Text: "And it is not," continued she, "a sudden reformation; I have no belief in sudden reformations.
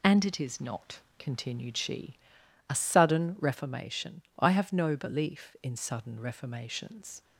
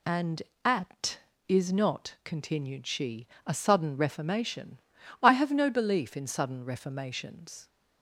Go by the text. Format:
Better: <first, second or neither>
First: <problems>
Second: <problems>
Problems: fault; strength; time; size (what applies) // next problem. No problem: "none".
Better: first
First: none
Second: says "at" for "it"; at 0.6 s